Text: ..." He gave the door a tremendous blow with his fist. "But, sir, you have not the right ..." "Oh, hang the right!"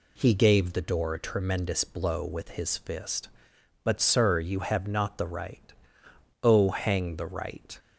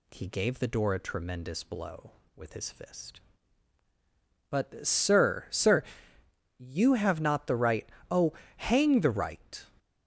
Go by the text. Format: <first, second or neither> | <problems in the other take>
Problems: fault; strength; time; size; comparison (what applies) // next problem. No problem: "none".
first | says "sir" twice; at 5.5 s